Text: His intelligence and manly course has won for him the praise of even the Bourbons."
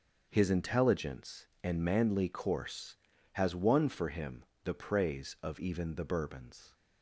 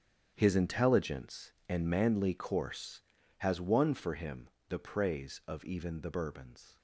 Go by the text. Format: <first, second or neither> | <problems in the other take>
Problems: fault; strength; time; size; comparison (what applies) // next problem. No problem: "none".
first | gets quieter; strong; throughout; 13 dB // starts louder than the rest; strong; until 1.3 s; 8.5 dB; also in the first // pauses between "him" and "the"; slight; at 4.4 s; 0.20 s long; slight in the first